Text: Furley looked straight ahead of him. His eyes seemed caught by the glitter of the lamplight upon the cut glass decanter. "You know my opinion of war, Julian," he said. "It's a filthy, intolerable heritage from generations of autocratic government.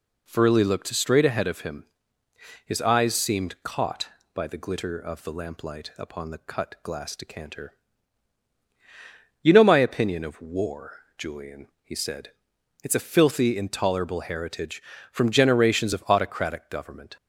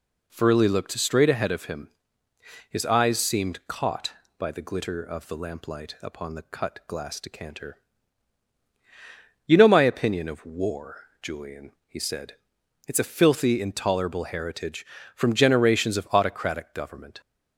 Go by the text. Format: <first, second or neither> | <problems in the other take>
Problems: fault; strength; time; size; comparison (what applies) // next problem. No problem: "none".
neither | none